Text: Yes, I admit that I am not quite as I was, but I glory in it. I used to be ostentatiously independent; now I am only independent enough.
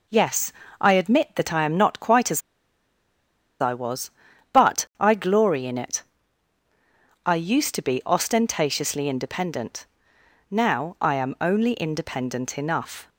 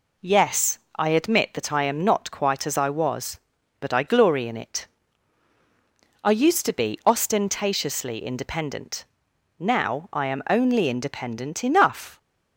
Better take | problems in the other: second | pauses between "as" and "I"; at 2.4 s; 1.1 s long

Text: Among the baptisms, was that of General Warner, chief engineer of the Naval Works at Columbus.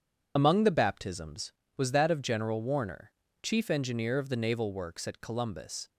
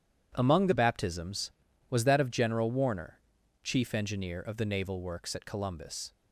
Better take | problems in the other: second | loses the start of "Among"; at 0.3 s; 50 ms

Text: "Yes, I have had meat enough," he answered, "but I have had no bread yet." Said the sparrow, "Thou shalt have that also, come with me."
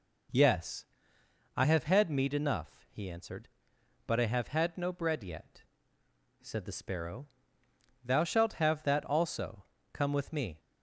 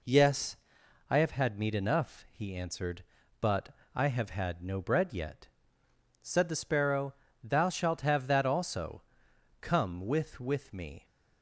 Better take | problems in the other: first | pauses between "but" and "I"; slight; at 3.6 s; 0.26 s long // says "with" twice; at 10.3 s

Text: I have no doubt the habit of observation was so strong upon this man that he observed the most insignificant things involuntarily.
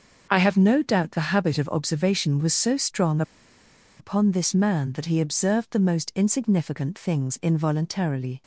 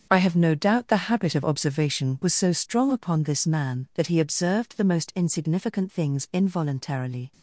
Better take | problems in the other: second | starts louder than the rest; until 1.3 s; 6.5 dB; strong in the second // pauses between "strong" and "upon"; noticeable; at 3.2 s; 0.77 s long

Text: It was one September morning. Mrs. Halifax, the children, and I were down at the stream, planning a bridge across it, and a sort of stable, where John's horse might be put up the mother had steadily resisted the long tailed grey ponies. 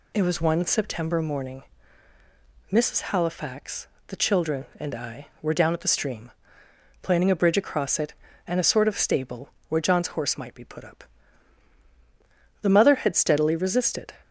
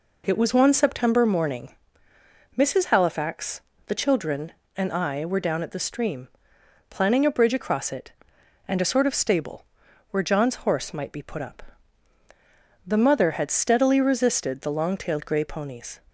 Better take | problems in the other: second | pauses between "up" and "the"; strong; at 11.0 s; 1.5 s long; also in the second // stops before "the long tailed grey ponies"; at 14.2 s

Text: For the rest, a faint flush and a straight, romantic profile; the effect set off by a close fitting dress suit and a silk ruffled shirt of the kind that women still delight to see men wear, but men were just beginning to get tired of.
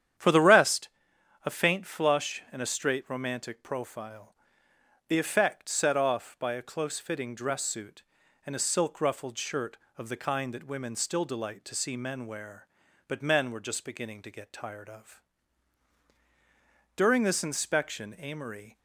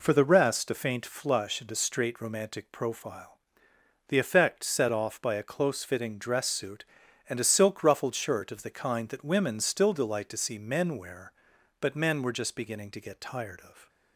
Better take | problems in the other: second | starts louder than the rest; strong; until 1.7 s; 9.5 dB // goes on to say "During this inspection Amory"; strong; from 16.9 s on; 1.8 s long

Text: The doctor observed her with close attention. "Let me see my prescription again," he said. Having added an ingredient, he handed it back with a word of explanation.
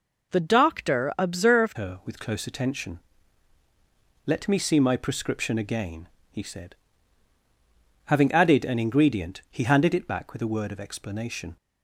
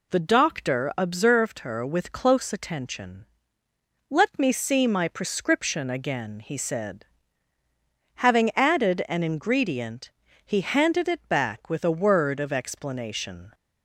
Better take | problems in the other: second | changes voice at "her"; from 1.7 s on; 9.8 s long

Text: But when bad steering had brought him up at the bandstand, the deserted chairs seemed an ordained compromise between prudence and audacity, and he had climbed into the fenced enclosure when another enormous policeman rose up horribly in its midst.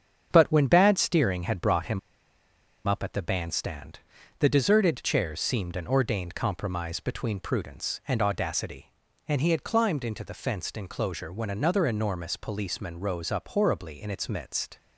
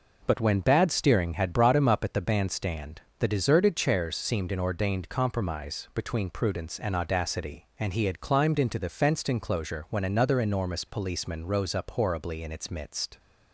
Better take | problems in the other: second | starts louder than the rest; strong; until 1.3 s; 7.5 dB // pauses between "him" and "up"; noticeable; at 1.9 s; 0.87 s long

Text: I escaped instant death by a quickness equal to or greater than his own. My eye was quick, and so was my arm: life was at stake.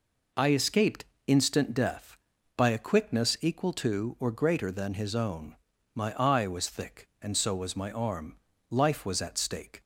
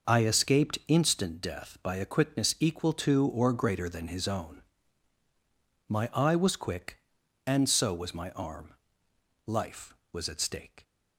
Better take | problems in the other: second | pauses between "escaped" and "instant"; slight; at 1.0 s; 0.22 s long // says "thick" for "quick"; at 6.7 s

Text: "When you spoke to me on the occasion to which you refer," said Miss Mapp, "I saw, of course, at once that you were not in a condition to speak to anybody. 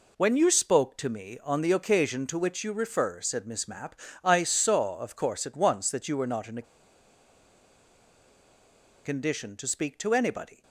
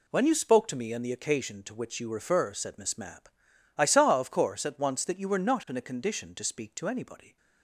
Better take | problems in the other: second | pauses between "a" and "condition"; strong; at 6.6 s; 2.4 s long

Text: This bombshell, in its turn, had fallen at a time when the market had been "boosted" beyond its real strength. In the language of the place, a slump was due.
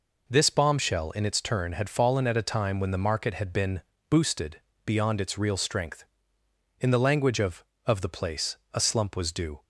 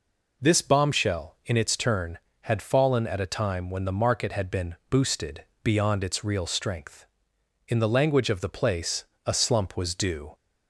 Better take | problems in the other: second | pauses between "been" and "boosted"; slight; at 3.8 s; 0.28 s long; slight in the second // pauses between "boosted" and "beyond"; slight; at 4.6 s; 0.24 s long; slight in the second // says "of" twice; at 7.8 s

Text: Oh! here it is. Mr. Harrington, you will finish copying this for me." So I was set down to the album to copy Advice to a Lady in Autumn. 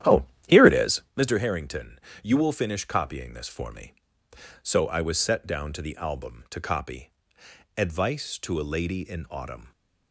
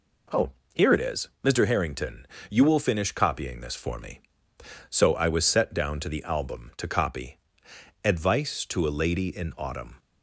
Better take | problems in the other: second | starts louder than the rest; strong; until 1.3 s; 11 dB // pauses between "copy" and "Advice"; noticeable; at 7.1 s; 0.66 s long; noticeable in the second

